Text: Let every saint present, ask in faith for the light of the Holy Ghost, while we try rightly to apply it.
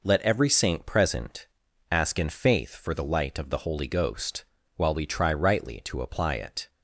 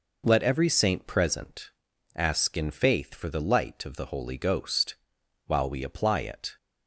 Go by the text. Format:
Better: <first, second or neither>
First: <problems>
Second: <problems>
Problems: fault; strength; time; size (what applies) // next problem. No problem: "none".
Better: first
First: none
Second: skips "try rightly to"; at 5.8 s